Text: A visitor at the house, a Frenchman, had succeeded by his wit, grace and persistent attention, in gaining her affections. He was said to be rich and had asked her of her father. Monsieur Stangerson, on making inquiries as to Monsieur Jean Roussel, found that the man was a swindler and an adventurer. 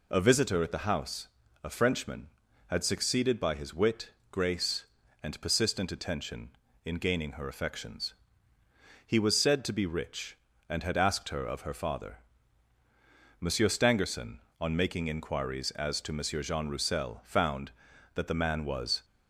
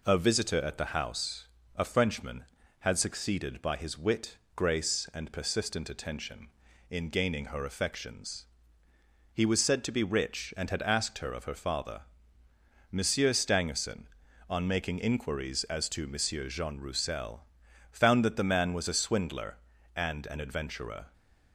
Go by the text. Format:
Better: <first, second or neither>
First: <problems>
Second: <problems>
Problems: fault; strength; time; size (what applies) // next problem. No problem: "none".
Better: second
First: stops before "a swindler and an adventurer"; at 19.0 s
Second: none